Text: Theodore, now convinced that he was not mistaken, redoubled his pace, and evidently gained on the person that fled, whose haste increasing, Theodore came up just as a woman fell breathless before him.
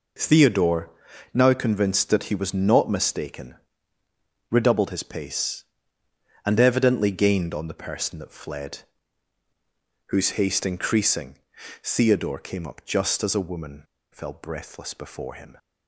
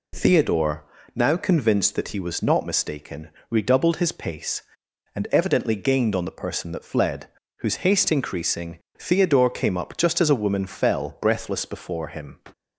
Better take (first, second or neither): second